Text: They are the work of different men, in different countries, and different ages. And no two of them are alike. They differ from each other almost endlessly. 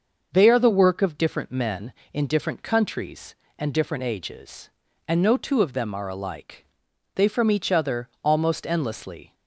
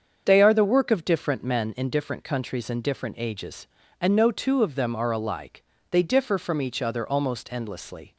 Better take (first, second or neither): second